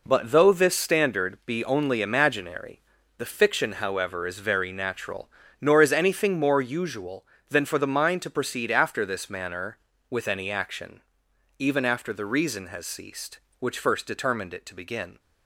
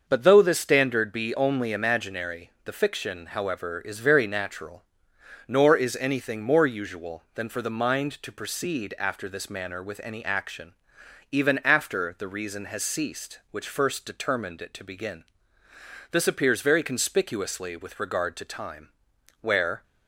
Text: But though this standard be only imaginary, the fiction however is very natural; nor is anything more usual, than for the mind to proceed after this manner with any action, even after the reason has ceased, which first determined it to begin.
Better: first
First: none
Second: starts louder than the rest; until 1.0 s; 6.5 dB // goes on to say "This appears very conspicuously with regard to time where"; strong; from 16.1 s on; 3.7 s long

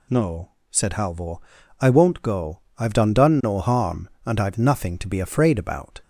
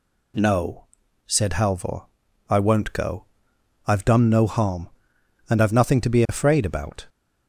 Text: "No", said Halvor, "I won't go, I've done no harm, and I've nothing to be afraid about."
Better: second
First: says "done" twice; at 3.1 s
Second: none

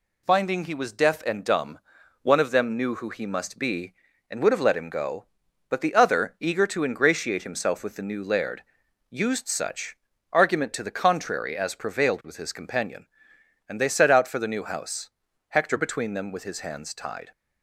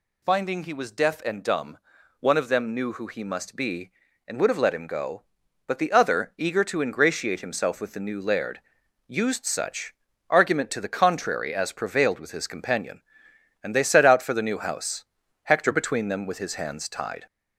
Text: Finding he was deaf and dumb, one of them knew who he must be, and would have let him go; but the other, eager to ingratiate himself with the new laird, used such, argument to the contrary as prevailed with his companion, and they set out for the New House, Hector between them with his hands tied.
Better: first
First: none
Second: gets louder; slight; throughout; 3 dB

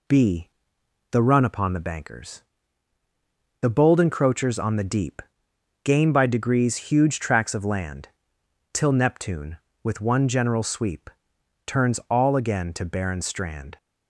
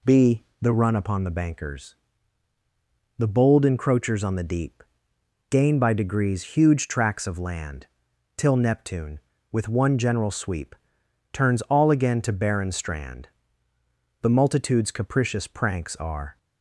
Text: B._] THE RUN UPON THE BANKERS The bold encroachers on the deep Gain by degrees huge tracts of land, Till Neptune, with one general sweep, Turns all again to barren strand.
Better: first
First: pauses between "BANKERS" and "The"; at 2.4 s; 1.1 s long // pauses between "deep" and "Gain"; noticeable; at 5.2 s; 0.64 s long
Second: pauses between "BANKERS" and "The"; at 1.9 s; 1.2 s long // pauses between "deep" and "Gain"; noticeable; at 4.8 s; 0.68 s long // goes on to say "The multitude's capricious pranks Are"; strong; from 14.2 s on; 2.1 s long

